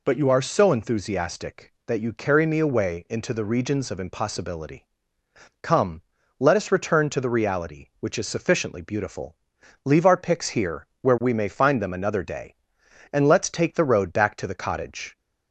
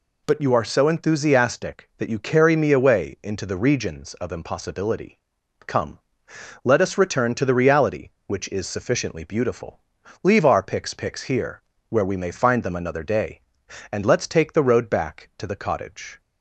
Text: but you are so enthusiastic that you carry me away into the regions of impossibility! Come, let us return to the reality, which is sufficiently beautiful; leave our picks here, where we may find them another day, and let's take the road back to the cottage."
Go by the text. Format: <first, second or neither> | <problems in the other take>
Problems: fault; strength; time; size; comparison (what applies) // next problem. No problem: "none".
first | says "picks" twice; at 10.9 s